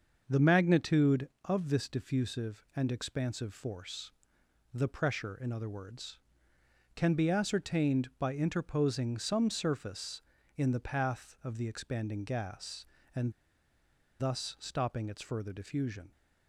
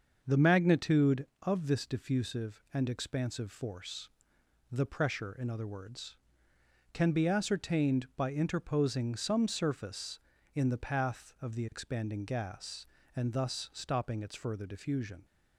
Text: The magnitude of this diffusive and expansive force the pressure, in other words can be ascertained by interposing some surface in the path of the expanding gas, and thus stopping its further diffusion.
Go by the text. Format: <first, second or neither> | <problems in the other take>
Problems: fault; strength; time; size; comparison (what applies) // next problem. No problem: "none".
second | starts louder than the rest; until 1.2 s; 6.5 dB; also in the second // pauses between "force" and "the"; noticeable; at 4.1 s; 0.62 s long; noticeable in the second // pauses between "and" and "thus"; noticeable; at 13.3 s; 0.87 s long